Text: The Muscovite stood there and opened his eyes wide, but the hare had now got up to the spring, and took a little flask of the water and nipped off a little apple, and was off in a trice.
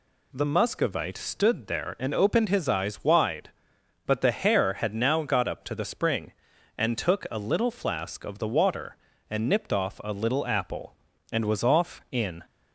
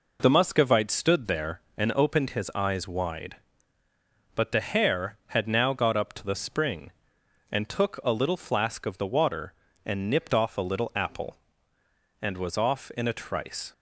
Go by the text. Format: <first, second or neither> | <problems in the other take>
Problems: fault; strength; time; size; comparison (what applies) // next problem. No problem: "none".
second | stops before "a trice"; at 12.4 s